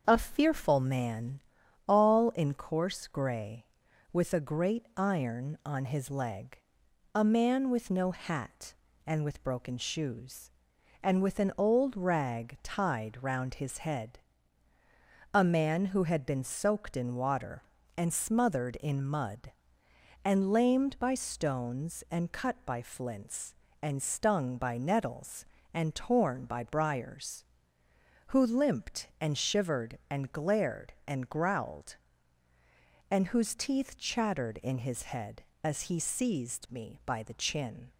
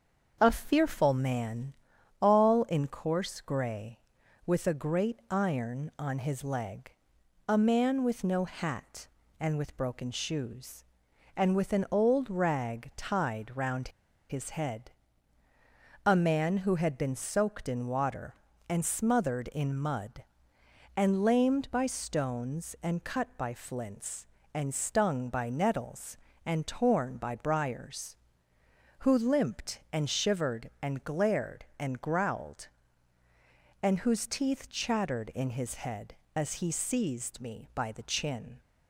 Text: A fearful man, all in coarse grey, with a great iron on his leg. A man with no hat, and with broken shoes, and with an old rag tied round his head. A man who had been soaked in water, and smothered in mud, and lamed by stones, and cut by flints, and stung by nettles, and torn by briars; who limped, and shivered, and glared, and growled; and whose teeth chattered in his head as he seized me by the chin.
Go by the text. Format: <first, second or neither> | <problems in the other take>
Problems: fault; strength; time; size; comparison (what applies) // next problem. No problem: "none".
first | starts louder than the rest; until 1.4 s; 6.5 dB; also in the first // pauses between "round" and "his"; at 13.8 s; 0.40 s long